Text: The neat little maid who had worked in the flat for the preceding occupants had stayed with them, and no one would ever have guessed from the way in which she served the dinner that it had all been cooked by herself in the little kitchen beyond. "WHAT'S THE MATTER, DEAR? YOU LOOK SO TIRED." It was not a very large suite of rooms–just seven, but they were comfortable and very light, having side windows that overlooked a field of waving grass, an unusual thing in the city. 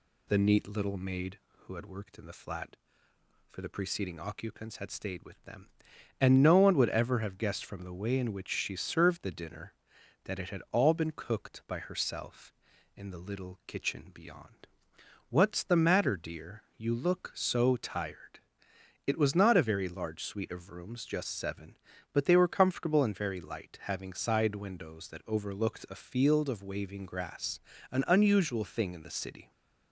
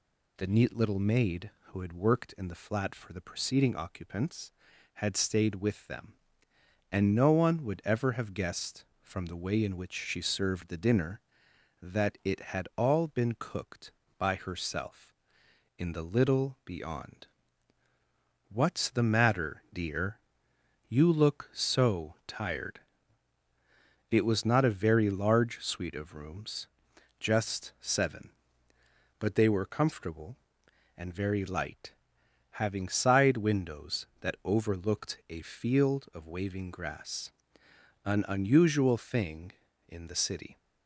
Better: first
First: none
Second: skips "kitchen"; at 16.5 s

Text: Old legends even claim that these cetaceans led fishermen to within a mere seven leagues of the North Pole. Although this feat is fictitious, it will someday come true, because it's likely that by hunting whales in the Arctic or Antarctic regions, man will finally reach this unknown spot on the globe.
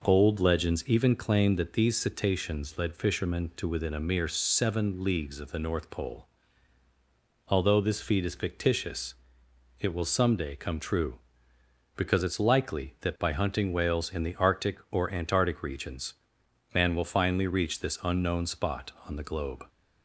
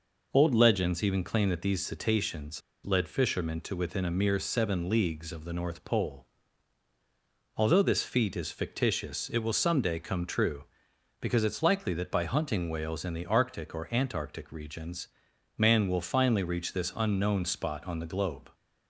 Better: first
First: none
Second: pauses between "cetaceans" and "led"; slight; at 2.6 s; 0.24 s long

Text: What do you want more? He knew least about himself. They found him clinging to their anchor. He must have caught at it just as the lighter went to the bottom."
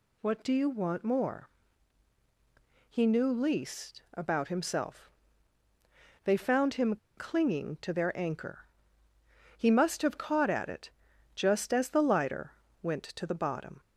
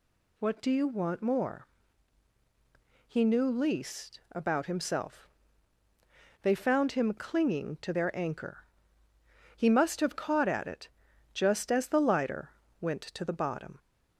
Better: second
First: pauses between "him" and "clinging"; slight; at 6.9 s; 0.21 s long // pauses between "it" and "just"; at 10.9 s; 0.44 s long // pauses between "lighter" and "went"; slight; at 12.5 s; 0.30 s long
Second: pauses between "it" and "just"; at 10.8 s; 0.44 s long // pauses between "lighter" and "went"; slight; at 12.5 s; 0.30 s long

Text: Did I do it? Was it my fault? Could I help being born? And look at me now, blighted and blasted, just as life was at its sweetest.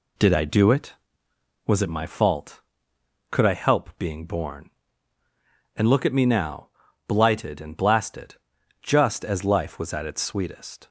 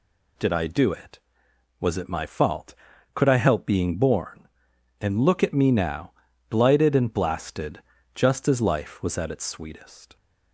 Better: neither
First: none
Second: none

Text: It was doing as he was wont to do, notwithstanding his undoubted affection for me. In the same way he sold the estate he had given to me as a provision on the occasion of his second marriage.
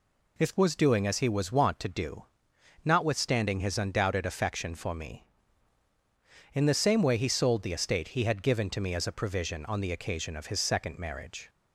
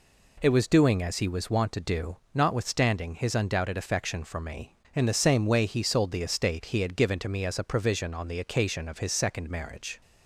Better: second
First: says "If" for "It"; at 0.3 s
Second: none

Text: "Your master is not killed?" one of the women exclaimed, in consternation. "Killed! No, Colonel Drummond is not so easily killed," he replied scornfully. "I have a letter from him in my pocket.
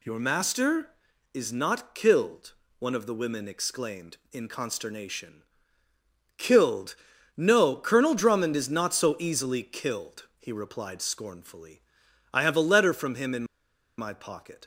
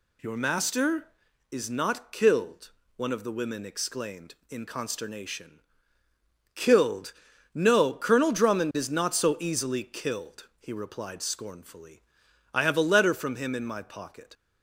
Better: second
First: pauses between "in" and "my"; noticeable; at 13.4 s; 0.54 s long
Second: none

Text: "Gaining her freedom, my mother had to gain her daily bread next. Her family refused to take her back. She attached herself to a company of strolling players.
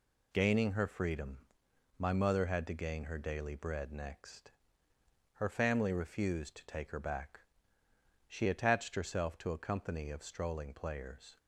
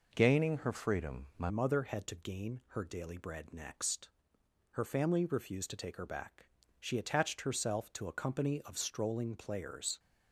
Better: first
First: none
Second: changes voice at "mother"; from 1.4 s on; 8.5 s long

